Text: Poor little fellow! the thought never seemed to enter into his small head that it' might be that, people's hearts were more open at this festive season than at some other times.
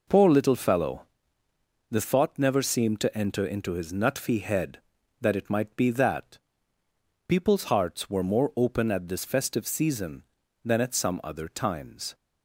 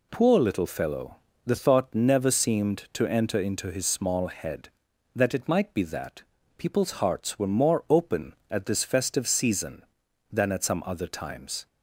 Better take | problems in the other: second | says "nutfy" for "small"; at 3.9 s

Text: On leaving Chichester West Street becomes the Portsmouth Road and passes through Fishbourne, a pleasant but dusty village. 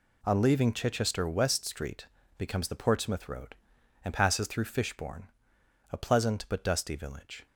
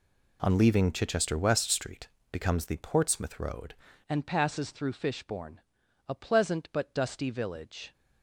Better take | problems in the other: first | pauses between "Street" and "becomes"; slight; at 2.0 s; 0.24 s long; slight in the first // changes voice at "and"; from 4.0 s on; 3.9 s long

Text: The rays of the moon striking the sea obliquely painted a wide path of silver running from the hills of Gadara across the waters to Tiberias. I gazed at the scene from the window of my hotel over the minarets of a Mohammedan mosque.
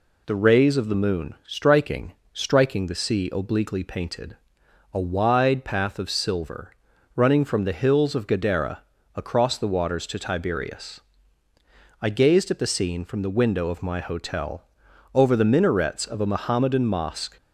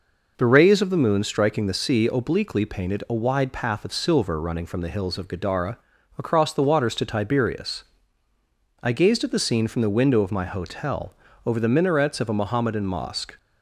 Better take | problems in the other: second | says "striking" twice; at 2.3 s // pauses between "painted" and "a"; noticeable; at 4.3 s; 0.54 s long // pauses between "silver" and "running"; at 6.7 s; 0.44 s long // pauses between "Gadara" and "across"; slight; at 8.7 s; 0.36 s long; also in the second // pauses between "hotel" and "over"; noticeable; at 14.6 s; 0.50 s long; slight in the second

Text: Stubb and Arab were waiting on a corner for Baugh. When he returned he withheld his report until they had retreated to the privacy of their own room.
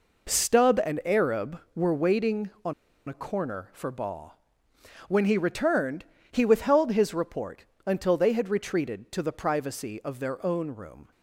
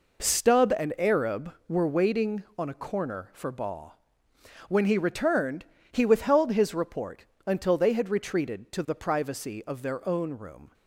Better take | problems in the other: second | pauses between "on" and "a"; slight; at 2.7 s; 0.35 s long // pauses between "returned" and "he"; slight; at 6.0 s; 0.26 s long; slight in the second // pauses between "report" and "until"; slight; at 7.6 s; 0.20 s long; slight in the second

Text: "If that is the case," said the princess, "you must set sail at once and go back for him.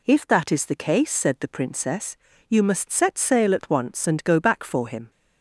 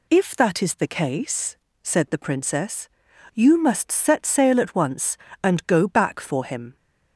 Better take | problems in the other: neither | none

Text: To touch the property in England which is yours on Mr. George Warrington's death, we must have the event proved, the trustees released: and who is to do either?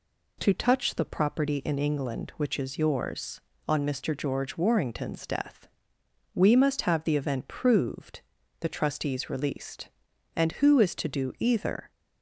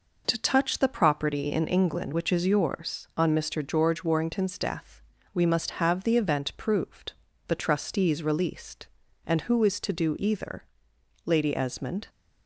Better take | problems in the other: first | goes on to say "Lady Esmond"; noticeable; from 11.2 s on; 0.82 s long

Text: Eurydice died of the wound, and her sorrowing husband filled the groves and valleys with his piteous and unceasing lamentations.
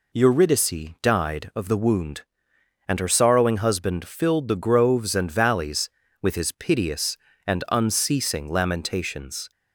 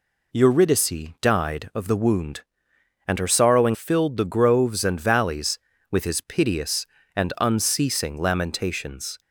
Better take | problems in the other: first | skips "husband"; at 3.7 s

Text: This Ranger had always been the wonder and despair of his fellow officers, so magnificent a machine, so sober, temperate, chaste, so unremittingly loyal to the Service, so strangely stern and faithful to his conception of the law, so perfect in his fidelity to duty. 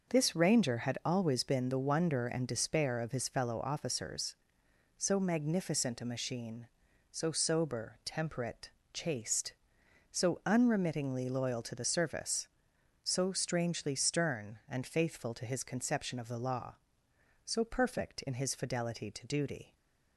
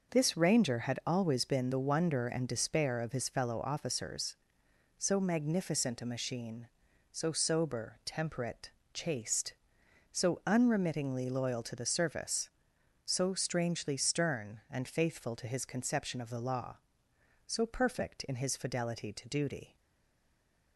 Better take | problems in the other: first | stays silent after the last word; from 19.7 s on; 1.0 s long

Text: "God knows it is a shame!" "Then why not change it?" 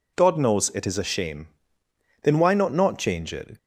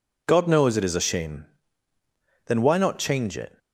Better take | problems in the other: second | says "not" twice; at 2.7 s

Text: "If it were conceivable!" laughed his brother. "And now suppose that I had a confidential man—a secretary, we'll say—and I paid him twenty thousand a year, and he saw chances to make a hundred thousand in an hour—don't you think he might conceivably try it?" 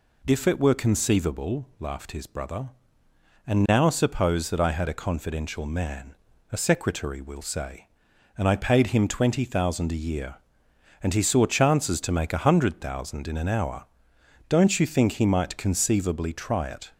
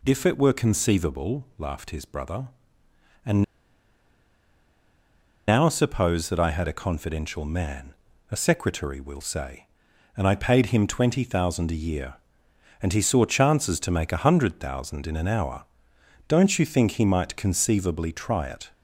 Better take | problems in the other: first | pauses between "And" and "now"; strong; at 3.4 s; 2.0 s long

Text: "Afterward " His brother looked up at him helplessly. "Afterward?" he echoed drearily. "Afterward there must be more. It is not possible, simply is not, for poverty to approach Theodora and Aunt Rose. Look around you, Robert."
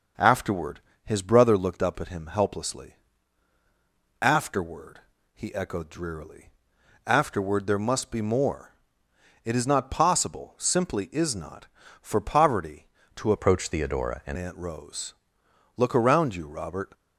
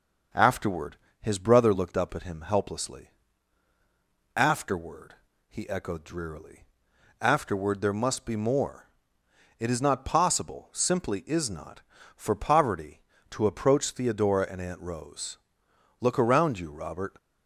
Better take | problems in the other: second | changes voice from "approach" to "and"; from 13.3 to 14.3 s; 1.0 s long

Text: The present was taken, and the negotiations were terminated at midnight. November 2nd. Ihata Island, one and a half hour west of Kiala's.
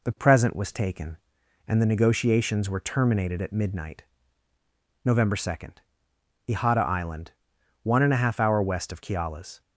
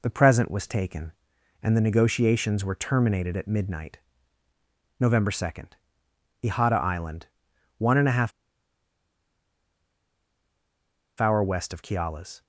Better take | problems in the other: first | pauses between "half" and "hour"; strong; at 8.3 s; 2.8 s long

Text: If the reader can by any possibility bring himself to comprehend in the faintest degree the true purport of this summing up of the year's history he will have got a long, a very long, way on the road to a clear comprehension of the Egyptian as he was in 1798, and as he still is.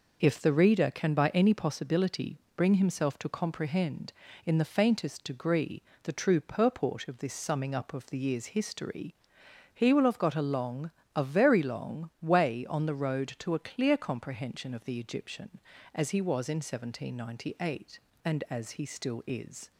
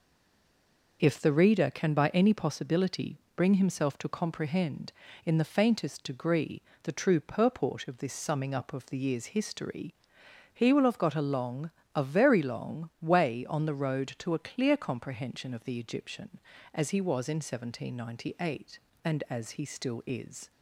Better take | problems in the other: first | stays silent before the first word; until 0.9 s; 0.9 s long // pauses between "possibility" and "bring"; slight; at 3.1 s; 0.18 s long; slight in the first // pauses between "degree" and "the"; slight; at 6.6 s; 0.22 s long; slight in the first // pauses between "history" and "he"; noticeable; at 9.9 s; 0.58 s long; noticeable in the first

